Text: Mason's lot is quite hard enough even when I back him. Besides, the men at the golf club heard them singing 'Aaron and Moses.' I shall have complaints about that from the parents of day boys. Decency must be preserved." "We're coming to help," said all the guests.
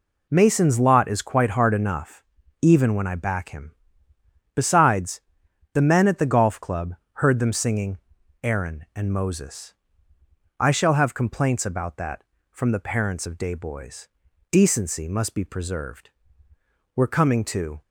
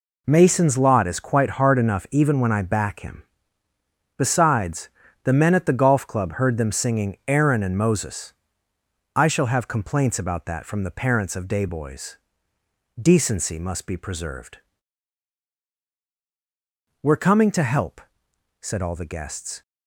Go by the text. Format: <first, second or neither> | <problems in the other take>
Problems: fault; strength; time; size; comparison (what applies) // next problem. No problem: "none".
second | pauses between "enough" and "even"; at 2.2 s; 0.40 s long // pauses between "club" and "heard"; slight; at 6.9 s; 0.22 s long // pauses between "singing" and "Aaron"; at 7.9 s; 0.44 s long // stops before "help said all the guests"; at 17.8 s